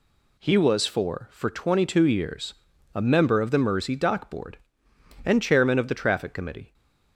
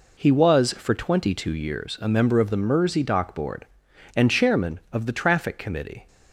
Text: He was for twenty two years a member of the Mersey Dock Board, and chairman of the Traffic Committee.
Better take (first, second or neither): second